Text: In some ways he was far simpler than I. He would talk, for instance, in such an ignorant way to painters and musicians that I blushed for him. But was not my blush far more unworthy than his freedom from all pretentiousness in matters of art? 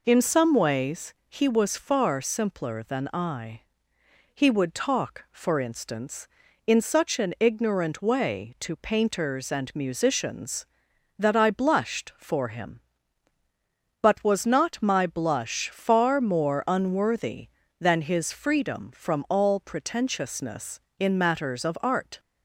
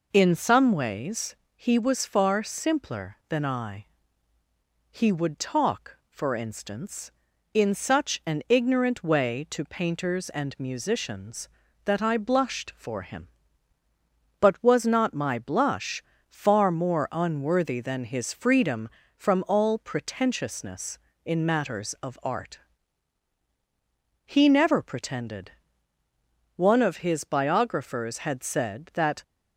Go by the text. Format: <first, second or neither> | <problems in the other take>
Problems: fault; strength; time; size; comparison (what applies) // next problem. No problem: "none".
first | pauses between "ways" and "he"; slight; at 1.3 s; 0.18 s long // pauses between "blush" and "far"; slight; at 16.0 s; 0.26 s long // goes on to say "He never pretended One of his biographers had said that"; strong; from 24.2 s on; 4.9 s long